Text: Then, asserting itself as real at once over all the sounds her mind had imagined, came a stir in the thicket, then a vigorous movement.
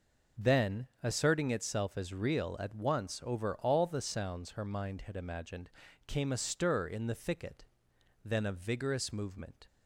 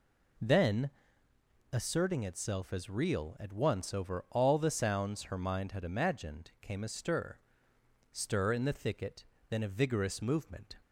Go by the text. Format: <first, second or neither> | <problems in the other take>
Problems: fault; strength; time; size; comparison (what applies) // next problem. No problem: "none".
first | says "stir" twice; at 8.0 s